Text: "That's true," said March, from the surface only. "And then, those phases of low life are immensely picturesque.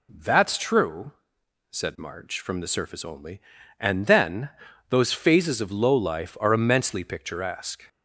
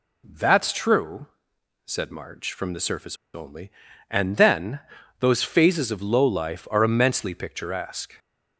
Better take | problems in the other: first | pauses between "surface" and "only"; slight; at 3.1 s; 0.19 s long

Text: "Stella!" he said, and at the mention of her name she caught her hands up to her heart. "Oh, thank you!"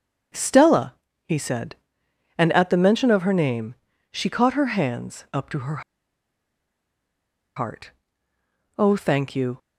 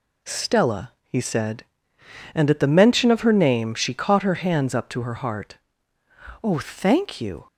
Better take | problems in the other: second | starts louder than the rest; strong; until 1.6 s; 7 dB // pauses between "name" and "she"; slight; at 3.7 s; 0.36 s long // pauses between "her" and "heart"; strong; at 5.8 s; 1.7 s long

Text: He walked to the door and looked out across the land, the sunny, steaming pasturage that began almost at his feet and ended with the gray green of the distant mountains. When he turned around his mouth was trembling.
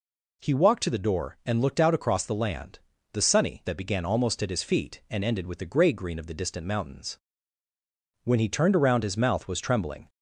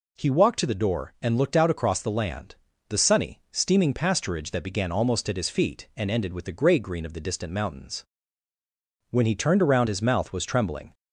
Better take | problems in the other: second | skips "steaming pasturage"; at 3.6 s

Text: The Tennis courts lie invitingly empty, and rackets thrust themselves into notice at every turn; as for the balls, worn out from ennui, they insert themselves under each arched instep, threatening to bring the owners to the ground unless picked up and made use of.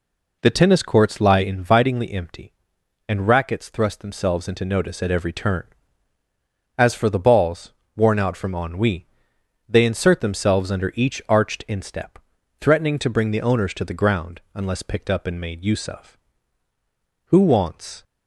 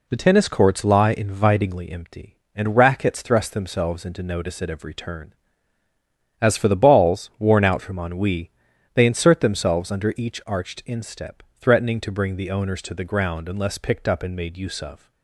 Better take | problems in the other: second | goes on to say "Who wants"; noticeable; from 17.2 s on; 0.74 s long

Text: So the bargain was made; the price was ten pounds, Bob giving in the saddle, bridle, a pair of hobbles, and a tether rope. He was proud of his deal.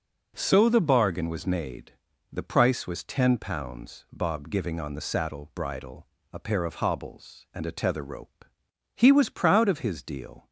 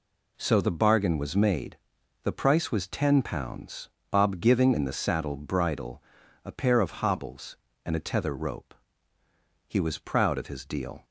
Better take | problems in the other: second | says "on" for "in"; at 4.8 s

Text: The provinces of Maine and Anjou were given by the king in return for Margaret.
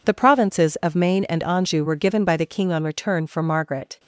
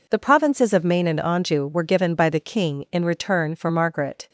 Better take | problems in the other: second | says "on" for "in"; at 2.7 s

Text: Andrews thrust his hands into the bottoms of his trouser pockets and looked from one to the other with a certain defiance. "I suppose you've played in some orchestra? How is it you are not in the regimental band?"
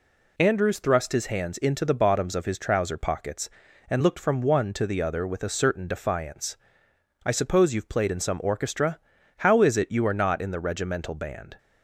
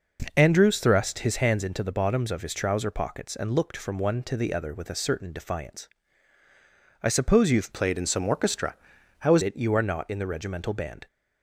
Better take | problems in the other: first | changes voice from "played" to "is"; from 7.7 to 9.4 s; 1.7 s long

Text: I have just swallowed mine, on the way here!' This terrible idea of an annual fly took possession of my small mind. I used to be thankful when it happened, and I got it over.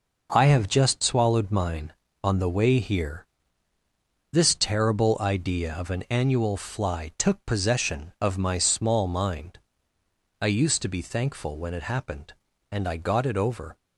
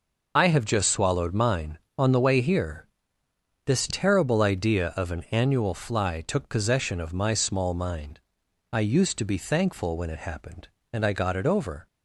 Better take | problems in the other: first | loses the start of "I"; at 0.3 s; 25 ms

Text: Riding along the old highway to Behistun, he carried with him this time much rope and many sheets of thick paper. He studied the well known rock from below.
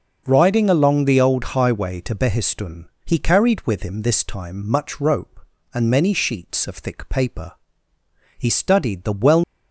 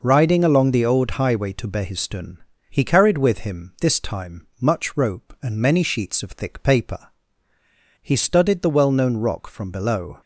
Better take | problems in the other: second | stops before "known rock from below"; at 9.4 s

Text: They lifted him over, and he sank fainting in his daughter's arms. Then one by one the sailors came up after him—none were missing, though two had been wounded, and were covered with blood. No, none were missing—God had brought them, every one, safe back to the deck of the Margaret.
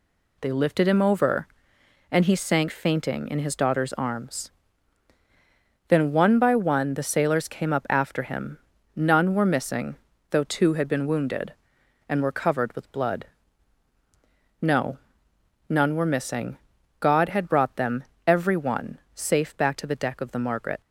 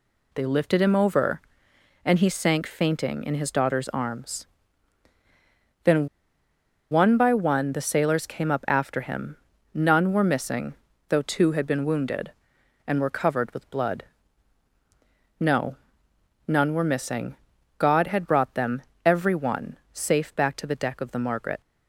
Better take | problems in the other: first | pauses between "Then" and "one"; noticeable; at 6.0 s; 0.83 s long

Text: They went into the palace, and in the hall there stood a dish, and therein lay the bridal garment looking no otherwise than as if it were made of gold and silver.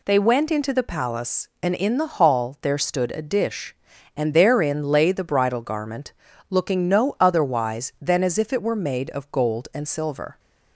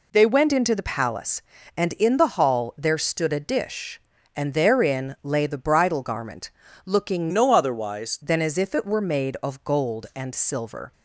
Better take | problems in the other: first | pauses between "garment" and "looking"; slight; at 6.4 s; 0.36 s long; also in the first // changes voice from "no" to "otherwise"; from 7.3 to 8.1 s; 0.8 s long

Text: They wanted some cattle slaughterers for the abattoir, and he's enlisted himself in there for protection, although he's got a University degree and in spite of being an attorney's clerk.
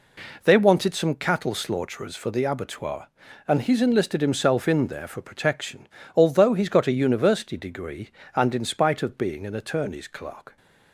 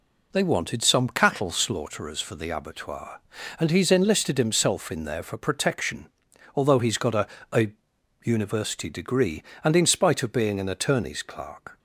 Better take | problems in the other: first | says "a" twice; at 7.5 s

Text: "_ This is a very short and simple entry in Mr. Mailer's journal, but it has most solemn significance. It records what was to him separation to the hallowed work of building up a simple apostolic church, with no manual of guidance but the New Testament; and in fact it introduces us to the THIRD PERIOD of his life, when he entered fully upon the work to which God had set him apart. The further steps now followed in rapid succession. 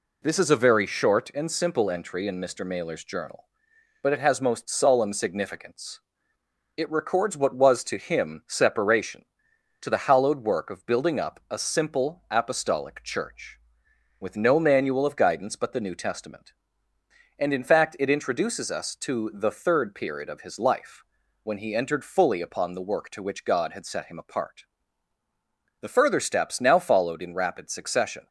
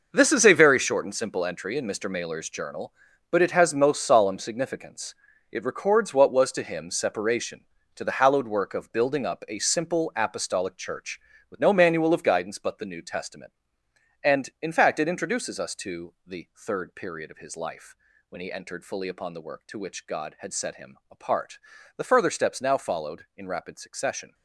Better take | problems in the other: first | gets quieter; strong; throughout; 12.5 dB

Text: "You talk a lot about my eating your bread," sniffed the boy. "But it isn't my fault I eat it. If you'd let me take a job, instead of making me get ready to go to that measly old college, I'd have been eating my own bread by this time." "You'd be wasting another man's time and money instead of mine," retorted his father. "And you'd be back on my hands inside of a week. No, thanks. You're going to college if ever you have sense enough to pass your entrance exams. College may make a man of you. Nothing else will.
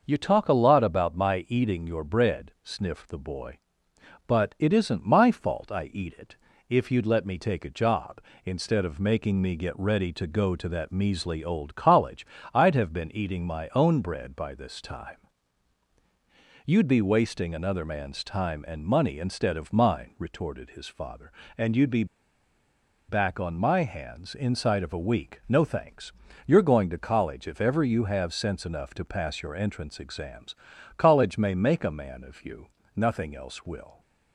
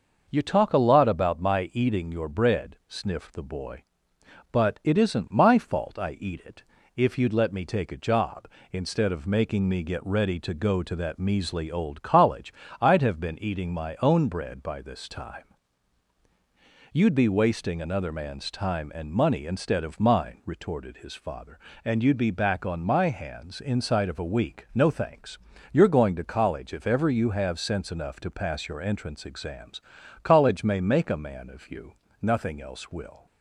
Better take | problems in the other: second | pauses between "be" and "back"; at 22.0 s; 1.0 s long

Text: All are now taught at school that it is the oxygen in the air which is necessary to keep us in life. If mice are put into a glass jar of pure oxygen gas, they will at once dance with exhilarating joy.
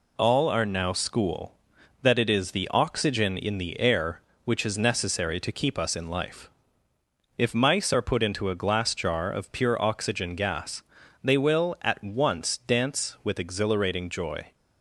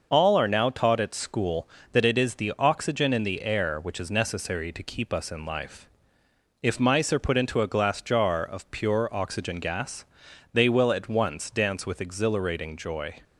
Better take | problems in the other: second | skips "taught at"; at 0.9 s

